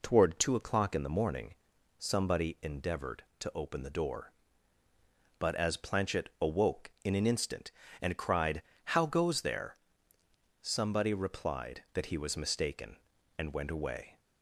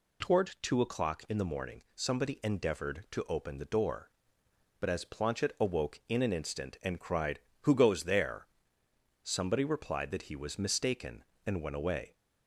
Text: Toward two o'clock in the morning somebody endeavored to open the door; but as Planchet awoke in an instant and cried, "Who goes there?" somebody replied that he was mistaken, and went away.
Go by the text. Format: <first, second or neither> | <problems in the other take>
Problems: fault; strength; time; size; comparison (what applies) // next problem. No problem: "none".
second | pauses between "morning" and "somebody"; noticeable; at 1.5 s; 0.46 s long // says "How" for "Who"; at 8.9 s